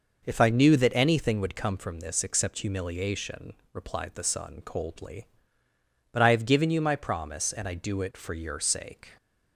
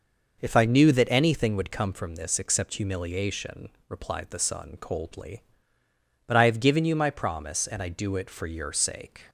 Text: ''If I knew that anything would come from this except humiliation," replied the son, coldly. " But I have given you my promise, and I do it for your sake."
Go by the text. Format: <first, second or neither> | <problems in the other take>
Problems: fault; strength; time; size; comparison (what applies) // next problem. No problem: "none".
neither | none